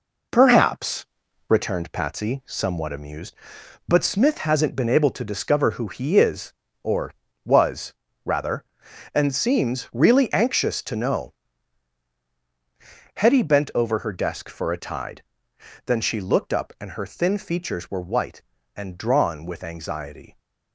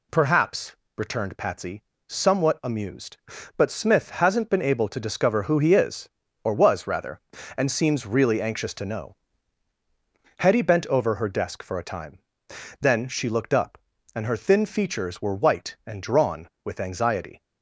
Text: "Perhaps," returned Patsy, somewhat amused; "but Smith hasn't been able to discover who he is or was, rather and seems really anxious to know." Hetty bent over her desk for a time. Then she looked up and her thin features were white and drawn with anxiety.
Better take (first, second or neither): second